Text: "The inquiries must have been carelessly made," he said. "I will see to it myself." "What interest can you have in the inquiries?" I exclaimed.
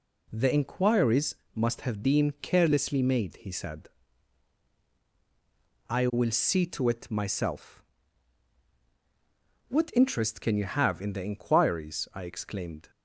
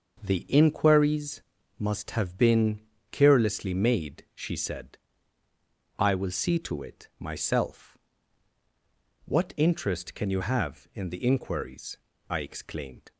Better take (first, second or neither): first